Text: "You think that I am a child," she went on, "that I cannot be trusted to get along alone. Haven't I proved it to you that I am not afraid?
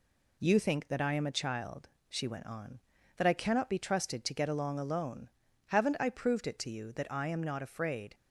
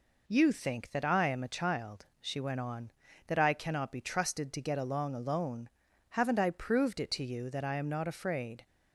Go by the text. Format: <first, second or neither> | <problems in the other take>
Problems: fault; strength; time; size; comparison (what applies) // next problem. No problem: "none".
neither | none